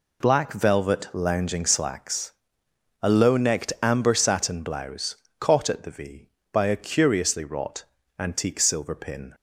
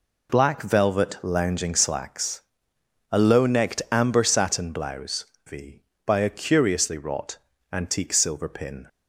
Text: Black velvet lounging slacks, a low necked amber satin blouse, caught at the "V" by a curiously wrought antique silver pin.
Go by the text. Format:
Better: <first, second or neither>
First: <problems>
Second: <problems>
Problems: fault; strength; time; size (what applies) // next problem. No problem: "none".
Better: first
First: pauses between "wrought" and "antique"; slight; at 7.8 s; 0.34 s long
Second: skips "caught at the"; at 5.3 s // pauses between "wrought" and "antique"; slight; at 7.3 s; 0.34 s long